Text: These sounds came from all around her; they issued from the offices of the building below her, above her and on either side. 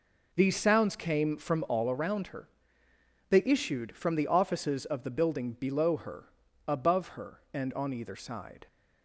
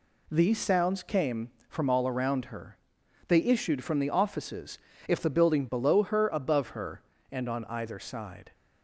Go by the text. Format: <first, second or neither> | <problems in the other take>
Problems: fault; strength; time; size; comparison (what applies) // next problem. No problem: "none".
first | says "if" for "of"; at 5.0 s